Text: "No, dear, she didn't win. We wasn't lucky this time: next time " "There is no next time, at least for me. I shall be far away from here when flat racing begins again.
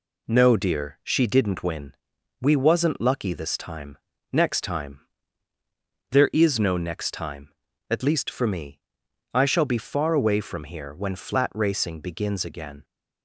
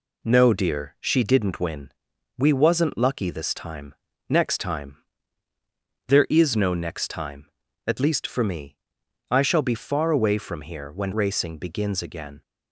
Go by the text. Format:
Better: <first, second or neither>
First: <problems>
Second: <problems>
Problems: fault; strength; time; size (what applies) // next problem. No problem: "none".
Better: first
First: none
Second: skips "flat"; at 11.1 s